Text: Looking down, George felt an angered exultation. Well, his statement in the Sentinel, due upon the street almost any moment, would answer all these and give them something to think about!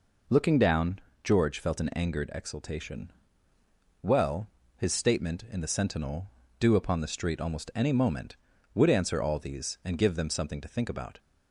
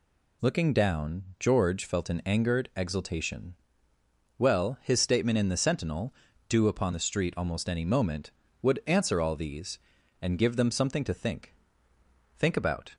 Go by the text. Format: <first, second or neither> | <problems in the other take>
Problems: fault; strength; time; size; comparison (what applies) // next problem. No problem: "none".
first | says "think" twice; at 12.3 s